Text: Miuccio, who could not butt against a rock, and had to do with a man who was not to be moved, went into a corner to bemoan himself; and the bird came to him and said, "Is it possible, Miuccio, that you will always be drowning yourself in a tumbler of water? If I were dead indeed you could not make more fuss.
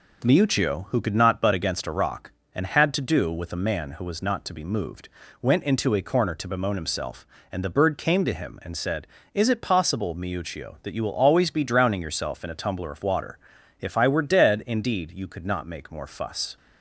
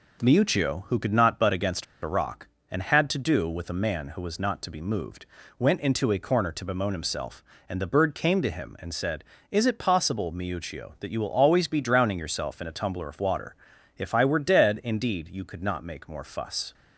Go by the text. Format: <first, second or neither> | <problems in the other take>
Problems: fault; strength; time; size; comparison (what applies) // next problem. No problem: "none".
first | pauses between "against" and "a"; slight; at 1.8 s; 0.18 s long